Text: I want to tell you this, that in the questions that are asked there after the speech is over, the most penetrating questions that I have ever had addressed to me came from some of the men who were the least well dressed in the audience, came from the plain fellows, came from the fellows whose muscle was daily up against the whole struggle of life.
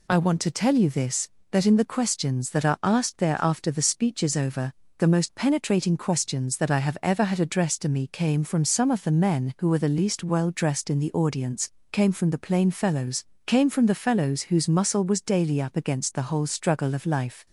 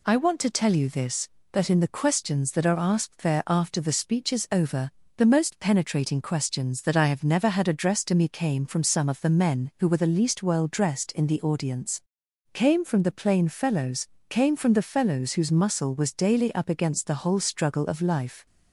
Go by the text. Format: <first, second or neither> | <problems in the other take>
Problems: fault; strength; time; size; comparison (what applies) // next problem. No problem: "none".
first | says "never" for "ever"; at 7.2 s